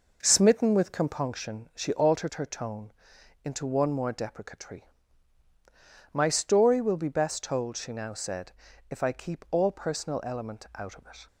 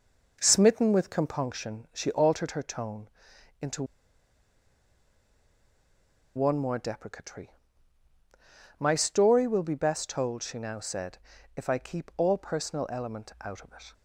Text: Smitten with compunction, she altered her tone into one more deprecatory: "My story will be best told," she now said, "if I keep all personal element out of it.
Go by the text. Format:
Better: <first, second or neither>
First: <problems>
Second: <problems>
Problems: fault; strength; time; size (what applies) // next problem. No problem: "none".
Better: first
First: pauses between "tone" and "into"; noticeable; at 2.9 s; 0.50 s long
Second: pauses between "tone" and "into"; noticeable; at 3.0 s; 0.50 s long // pauses between "into" and "one"; strong; at 3.8 s; 2.5 s long